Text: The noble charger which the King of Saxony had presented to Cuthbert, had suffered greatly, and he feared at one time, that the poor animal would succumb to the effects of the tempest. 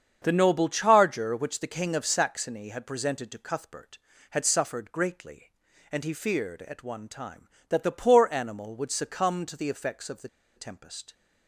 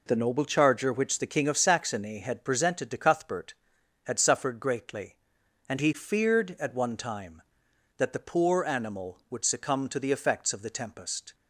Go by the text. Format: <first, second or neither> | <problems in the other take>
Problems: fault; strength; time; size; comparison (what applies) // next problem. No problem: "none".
second | starts louder than the rest; strong; until 1.2 s; 7.5 dB // pauses between "the" and "tempest"; slight; at 10.2 s; 0.27 s long